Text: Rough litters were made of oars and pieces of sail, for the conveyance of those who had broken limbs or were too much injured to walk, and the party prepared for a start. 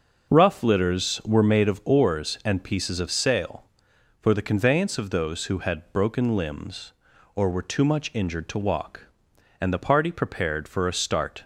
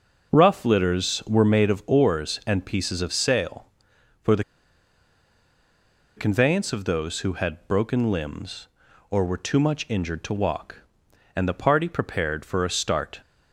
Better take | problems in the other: first | pauses between "the" and "conveyance"; strong; at 4.4 s; 1.7 s long

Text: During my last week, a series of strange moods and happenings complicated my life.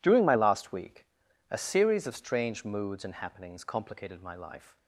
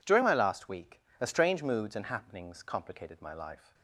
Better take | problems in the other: first | skips "series of"; at 1.2 s

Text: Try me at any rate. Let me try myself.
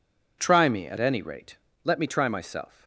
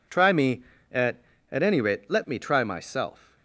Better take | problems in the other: first | says "at" twice; at 1.4 s

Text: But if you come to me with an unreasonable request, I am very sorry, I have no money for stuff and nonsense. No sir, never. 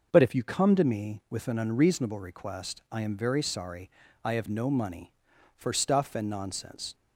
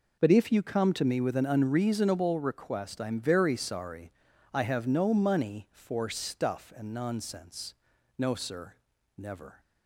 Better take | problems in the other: second | stops before "No sir never"; at 6.9 s

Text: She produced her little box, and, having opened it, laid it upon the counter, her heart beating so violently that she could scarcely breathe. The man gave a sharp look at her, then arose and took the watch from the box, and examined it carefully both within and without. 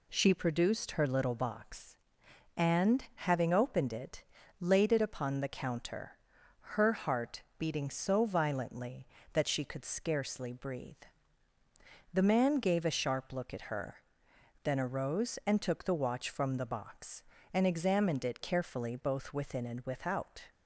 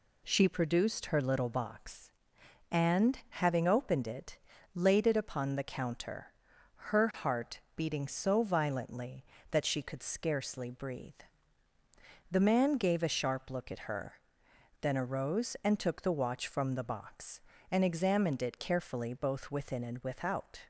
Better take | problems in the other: neither | pauses between "heart" and "beating"; slight; the same in both

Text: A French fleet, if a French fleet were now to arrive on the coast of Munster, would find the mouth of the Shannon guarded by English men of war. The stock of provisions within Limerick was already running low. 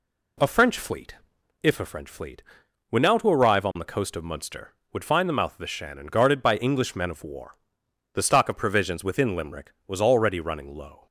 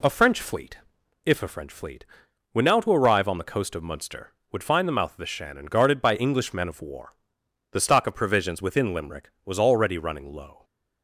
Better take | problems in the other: neither | none

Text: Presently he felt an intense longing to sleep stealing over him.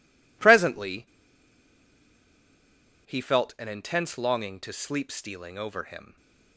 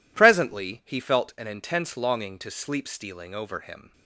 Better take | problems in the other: second | pauses between "Presently" and "he"; strong; at 1.0 s; 2.0 s long

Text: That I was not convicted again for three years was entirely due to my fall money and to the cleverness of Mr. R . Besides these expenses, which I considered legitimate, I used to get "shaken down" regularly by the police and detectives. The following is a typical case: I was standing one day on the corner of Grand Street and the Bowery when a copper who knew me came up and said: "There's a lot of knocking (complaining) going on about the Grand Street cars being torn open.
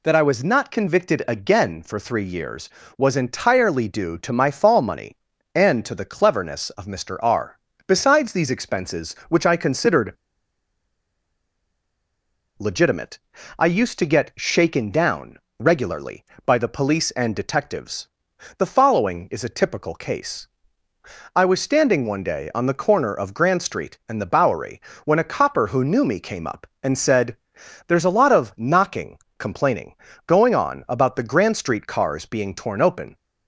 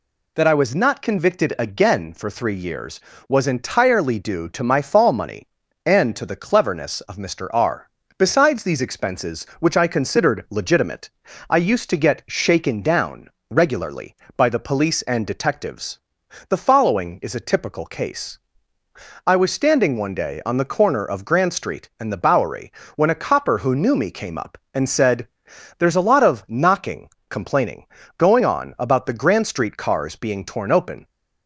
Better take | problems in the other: second | pauses between "considered" and "legitimate"; strong; at 10.1 s; 2.4 s long // pauses between "down" and "regularly"; slight; at 15.3 s; 0.22 s long; slight in the second // pauses between "Bowery" and "when"; slight; at 24.8 s; 0.24 s long; slight in the second

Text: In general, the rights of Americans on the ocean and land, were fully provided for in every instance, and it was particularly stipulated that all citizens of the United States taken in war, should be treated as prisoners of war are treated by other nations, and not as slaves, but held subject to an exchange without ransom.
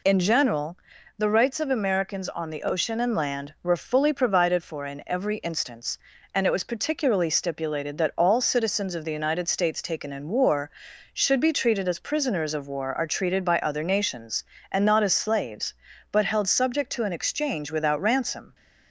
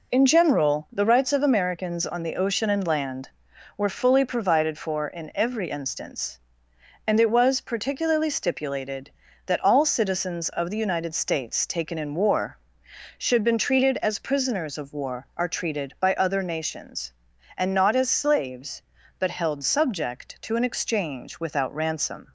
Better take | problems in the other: first | says "been" for "be"; at 13.4 s

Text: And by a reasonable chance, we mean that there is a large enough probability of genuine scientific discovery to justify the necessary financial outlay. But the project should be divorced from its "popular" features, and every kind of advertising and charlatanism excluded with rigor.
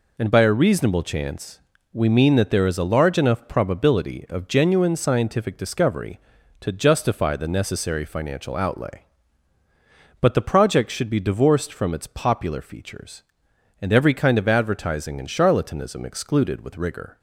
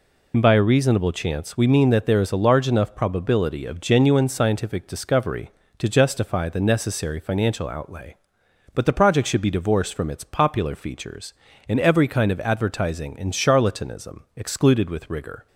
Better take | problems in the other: first | loses the start of "And"; at 0.3 s; 55 ms

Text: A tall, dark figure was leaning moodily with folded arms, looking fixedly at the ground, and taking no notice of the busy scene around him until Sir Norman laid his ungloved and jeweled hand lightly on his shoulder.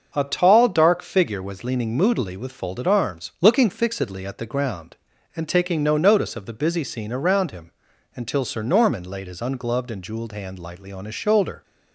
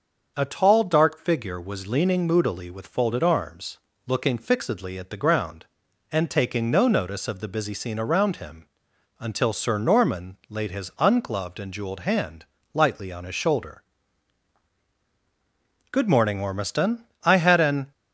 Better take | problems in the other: first | starts louder than the rest; until 1.3 s; 6.5 dB; also in the first // pauses between "him" and "until"; noticeable; at 8.6 s; 0.52 s long; also in the first // pauses between "hand" and "lightly"; slight; at 12.4 s; 0.28 s long // goes on to say "Good morning Ormiston I had an"; strong; from 15.9 s on; 2.0 s long

